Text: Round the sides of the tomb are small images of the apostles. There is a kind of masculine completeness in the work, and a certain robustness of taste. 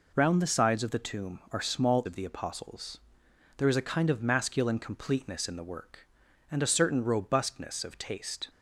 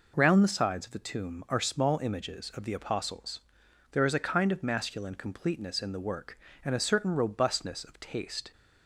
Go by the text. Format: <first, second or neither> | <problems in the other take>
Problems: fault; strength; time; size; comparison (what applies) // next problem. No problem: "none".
second | skips "images"; at 2.0 s